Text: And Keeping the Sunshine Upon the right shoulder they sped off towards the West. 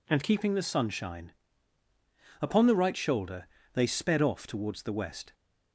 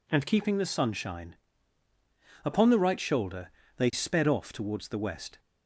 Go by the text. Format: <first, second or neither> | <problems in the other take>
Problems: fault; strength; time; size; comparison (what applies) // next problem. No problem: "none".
neither | pauses between "Sunshine" and "Upon"; the same in both // pauses between "shoulder" and "they"; slight; the same in both